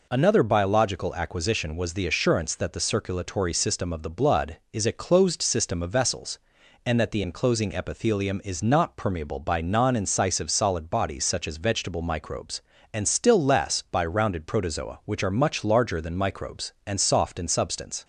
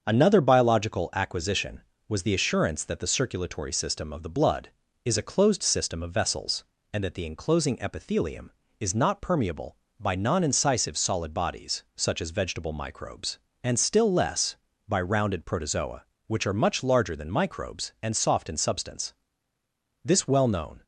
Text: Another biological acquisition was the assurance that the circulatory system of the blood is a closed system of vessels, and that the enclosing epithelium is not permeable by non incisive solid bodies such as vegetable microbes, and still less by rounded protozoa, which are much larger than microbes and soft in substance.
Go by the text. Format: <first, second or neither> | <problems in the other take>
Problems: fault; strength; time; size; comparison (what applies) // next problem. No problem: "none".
first | starts louder than the rest; until 1.0 s; 7 dB // goes on to say "This well known"; noticeable; from 20.0 s on; 0.80 s long